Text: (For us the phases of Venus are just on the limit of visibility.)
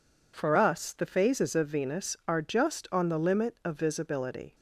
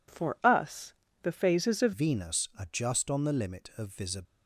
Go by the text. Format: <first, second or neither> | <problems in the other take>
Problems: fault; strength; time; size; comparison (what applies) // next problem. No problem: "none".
first | pauses between "us" and "the"; slight; at 0.9 s; 0.26 s long // changes voice at "Venus"; from 1.9 s on; 2.3 s long